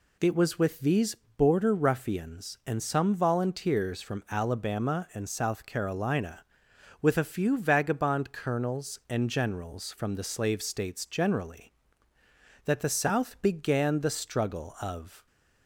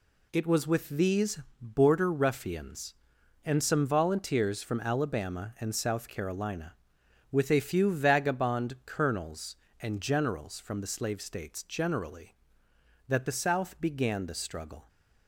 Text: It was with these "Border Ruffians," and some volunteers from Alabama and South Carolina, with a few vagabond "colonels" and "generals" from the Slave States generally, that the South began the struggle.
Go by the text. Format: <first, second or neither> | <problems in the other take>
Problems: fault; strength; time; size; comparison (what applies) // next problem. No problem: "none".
second | pauses between "these" and "Border"; slight; at 1.1 s; 0.22 s long; slight in the second // goes on to say "Of"; slight; from 14.7 s on; 0.46 s long